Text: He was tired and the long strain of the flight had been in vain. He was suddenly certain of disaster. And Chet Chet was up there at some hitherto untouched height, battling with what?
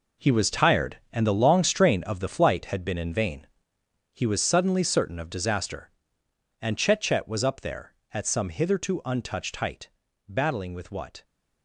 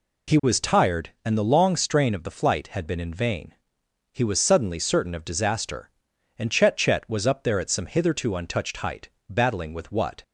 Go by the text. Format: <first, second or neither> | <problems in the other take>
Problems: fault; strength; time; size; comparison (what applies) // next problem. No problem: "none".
second | gets quieter; strong; throughout; 12 dB